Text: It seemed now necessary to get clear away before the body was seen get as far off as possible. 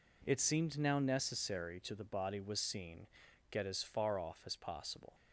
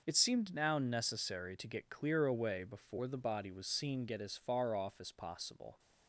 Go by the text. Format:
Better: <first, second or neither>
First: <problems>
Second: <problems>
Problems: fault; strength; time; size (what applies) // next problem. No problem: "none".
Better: second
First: skips "get clear away before"; at 1.9 s // pauses between "seen" and "get"; at 3.0 s; 0.44 s long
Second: none